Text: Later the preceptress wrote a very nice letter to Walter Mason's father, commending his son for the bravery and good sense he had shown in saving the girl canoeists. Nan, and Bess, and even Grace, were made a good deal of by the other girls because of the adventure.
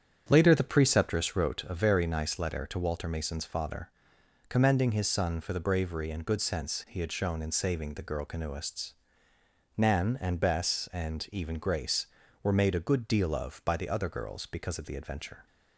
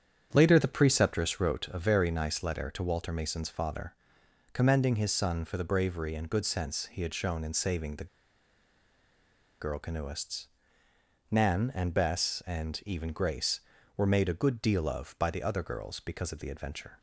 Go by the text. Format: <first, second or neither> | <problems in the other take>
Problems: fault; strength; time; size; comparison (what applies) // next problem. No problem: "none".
first | starts louder than the rest; strong; until 1.3 s; 8.5 dB; strong in the first // pauses between "the" and "girl"; strong; at 8.0 s; 1.5 s long